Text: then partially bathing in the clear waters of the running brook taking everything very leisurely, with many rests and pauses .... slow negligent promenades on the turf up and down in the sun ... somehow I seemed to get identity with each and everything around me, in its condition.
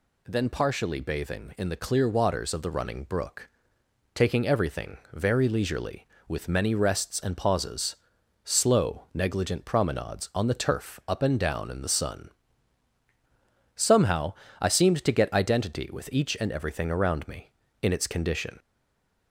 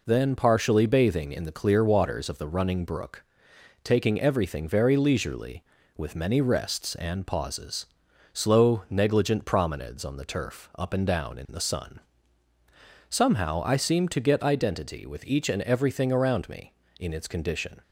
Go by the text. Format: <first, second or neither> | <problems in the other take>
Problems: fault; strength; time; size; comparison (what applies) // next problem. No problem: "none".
second | pauses between "brook" and "taking"; noticeable; at 3.4 s; 0.66 s long; noticeable in the second // pauses between "everything" and "very"; slight; at 4.9 s; 0.16 s long // pauses between "somehow" and "I"; slight; at 14.3 s; 0.26 s long // stays silent after the last word; slight; from 18.5 s on; 0.7 s long